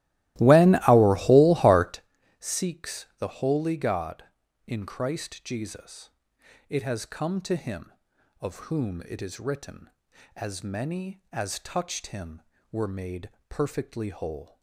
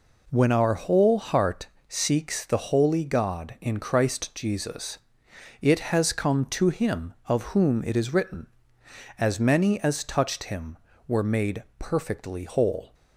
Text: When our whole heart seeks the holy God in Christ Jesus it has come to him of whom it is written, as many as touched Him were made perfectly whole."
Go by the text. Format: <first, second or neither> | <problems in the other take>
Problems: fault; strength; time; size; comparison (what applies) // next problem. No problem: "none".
second | starts louder than the rest; strong; until 2.1 s; 17 dB // pauses between "heart" and "seeks"; at 2.0 s; 0.38 s long; slight in the second // pauses between "Jesus" and "it"; noticeable; at 6.1 s; 0.58 s long; noticeable in the second // pauses between "made" and "perfectly"; slight; at 13.3 s; 0.18 s long